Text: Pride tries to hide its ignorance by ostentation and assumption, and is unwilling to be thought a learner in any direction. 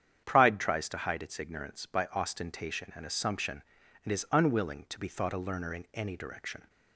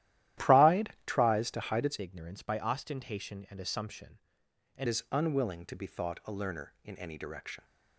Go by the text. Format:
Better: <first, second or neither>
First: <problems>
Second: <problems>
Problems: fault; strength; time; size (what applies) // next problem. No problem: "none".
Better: first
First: starts louder than the rest; strong; until 1.2 s; 8.5 dB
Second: starts louder than the rest; strong; until 1.4 s; 13.5 dB // changes voice from "ignorance" to "and"; from 1.9 to 4.8 s; 2.9 s long